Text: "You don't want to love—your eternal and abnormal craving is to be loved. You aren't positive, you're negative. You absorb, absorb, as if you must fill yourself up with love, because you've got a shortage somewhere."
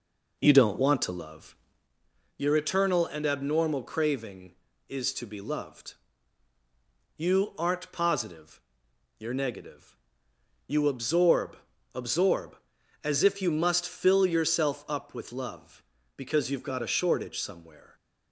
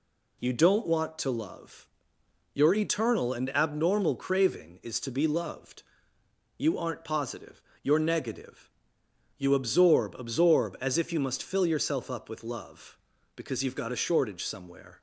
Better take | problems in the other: second | starts louder than the rest; noticeable; until 1.9 s; 4.5 dB

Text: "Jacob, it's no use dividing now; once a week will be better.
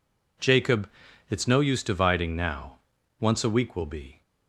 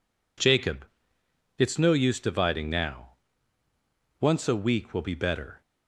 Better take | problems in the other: second | stops before "better"; at 4.2 s

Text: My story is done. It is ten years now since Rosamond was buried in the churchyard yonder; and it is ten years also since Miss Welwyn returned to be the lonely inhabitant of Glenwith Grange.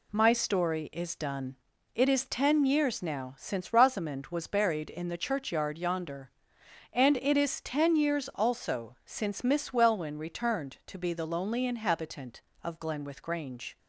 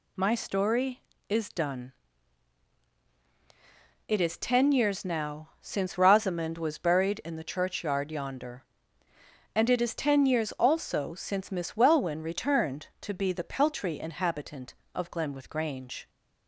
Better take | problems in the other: first | says "peltry" for "lonely"; at 13.4 s

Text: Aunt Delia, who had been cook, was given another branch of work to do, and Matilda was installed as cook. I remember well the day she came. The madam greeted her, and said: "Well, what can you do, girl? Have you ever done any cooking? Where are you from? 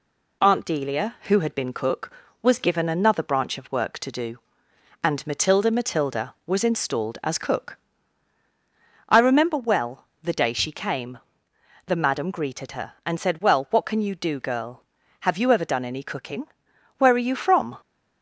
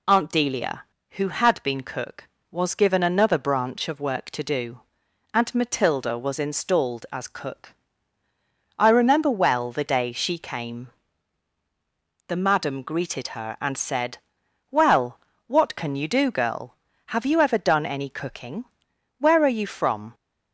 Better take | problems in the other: second | says "Matilda" twice; at 5.6 s // pauses between "well" and "the"; slight; at 10.0 s; 0.18 s long

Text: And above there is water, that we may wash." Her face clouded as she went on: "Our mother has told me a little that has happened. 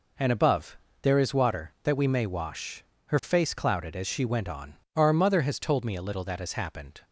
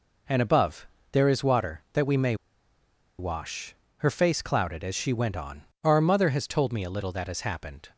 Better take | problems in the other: first | pauses between "above" and "there"; slight; at 0.8 s; 0.26 s long; slight in the first // pauses between "may" and "wash"; noticeable; at 2.3 s; 0.84 s long

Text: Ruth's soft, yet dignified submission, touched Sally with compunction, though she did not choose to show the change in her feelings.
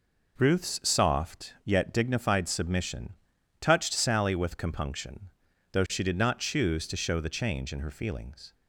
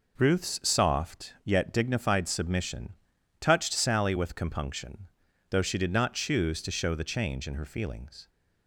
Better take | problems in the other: neither | none

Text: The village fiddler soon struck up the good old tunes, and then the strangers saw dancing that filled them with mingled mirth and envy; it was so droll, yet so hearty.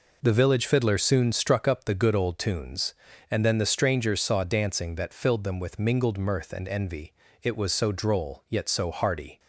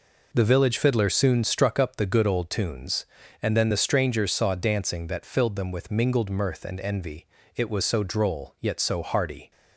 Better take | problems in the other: neither | none

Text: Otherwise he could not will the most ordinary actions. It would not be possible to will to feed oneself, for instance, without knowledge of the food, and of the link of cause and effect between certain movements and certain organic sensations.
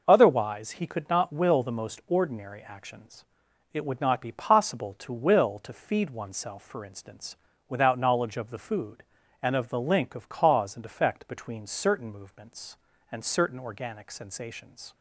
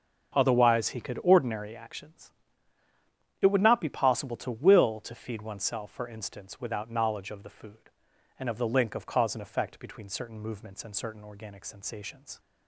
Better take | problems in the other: first | starts louder than the rest; until 1.4 s; 6.5 dB // skips "not will the most"; at 1.2 s

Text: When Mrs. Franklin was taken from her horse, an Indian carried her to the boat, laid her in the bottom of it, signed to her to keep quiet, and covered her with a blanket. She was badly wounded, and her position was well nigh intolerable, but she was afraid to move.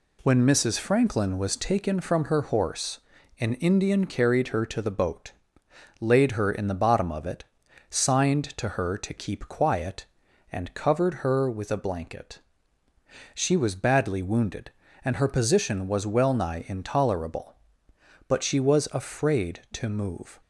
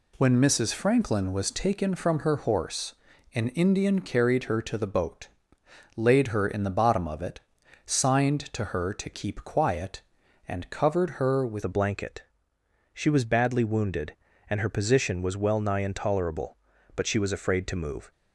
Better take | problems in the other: first | changes voice at "a"; from 11.6 s on; 6.5 s long

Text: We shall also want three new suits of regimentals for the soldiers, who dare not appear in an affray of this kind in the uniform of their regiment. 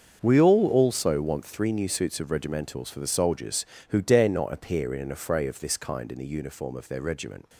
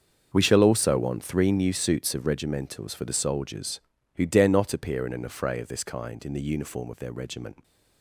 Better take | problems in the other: second | starts louder than the rest; until 1.2 s; 6.5 dB; also in the second // says "all" for "shall"; at 0.4 s

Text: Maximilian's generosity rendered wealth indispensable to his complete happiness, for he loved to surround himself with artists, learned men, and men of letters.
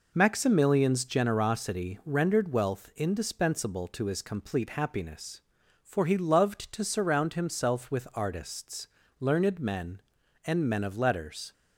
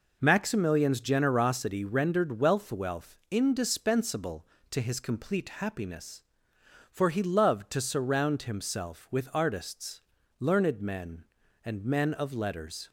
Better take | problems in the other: first | says "wealth" twice; at 2.7 s

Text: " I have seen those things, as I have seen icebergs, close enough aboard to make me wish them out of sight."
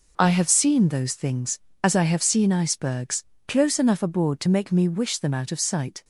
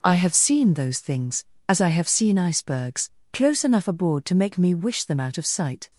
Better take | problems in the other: neither | none

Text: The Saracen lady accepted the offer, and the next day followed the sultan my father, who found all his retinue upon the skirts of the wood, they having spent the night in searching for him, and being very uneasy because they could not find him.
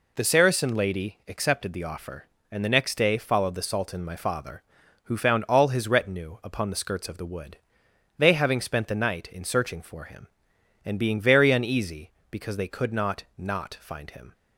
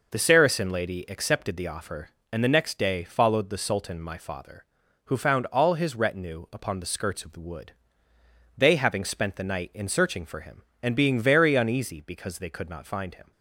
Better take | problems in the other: second | says "not" twice; at 13.3 s

